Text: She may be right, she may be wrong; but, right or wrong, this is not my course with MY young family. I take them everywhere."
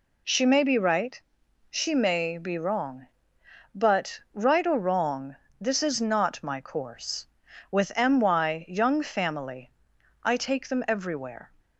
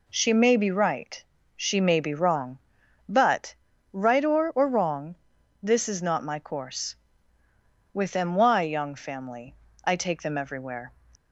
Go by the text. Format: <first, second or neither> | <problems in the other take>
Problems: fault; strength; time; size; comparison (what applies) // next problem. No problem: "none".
first | says "or" twice; at 4.5 s